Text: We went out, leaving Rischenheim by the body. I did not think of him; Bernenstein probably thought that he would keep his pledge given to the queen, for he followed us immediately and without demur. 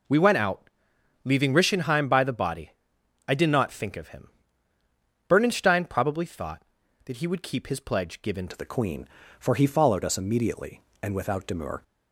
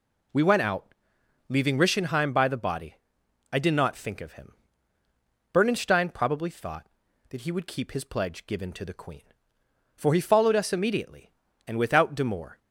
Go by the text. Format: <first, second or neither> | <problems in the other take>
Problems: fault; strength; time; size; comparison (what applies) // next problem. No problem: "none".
second | changes voice at "to"; from 8.4 s on; 3.4 s long